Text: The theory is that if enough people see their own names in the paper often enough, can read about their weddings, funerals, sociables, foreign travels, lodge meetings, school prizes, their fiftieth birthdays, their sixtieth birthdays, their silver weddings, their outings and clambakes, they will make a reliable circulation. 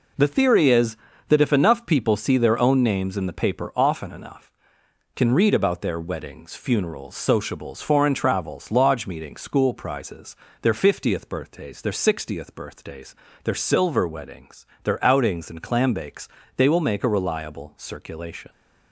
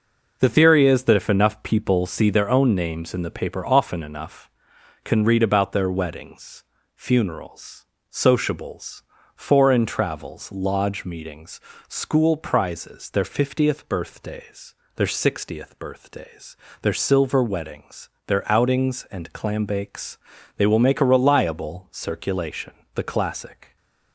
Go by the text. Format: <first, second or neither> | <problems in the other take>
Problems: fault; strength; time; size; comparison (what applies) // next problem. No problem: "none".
first | goes on to say "The classic"; noticeable; from 22.9 s on; 0.82 s long